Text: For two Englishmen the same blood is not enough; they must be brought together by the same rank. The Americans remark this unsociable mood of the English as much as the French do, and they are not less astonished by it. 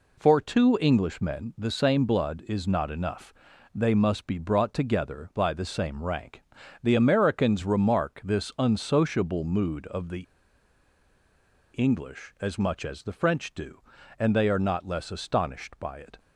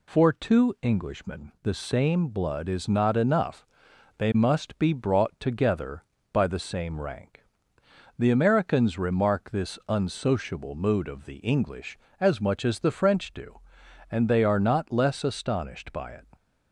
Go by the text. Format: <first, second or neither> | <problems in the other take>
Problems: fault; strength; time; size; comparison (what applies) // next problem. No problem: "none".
second | pauses between "the" and "English"; strong; at 10.2 s; 1.5 s long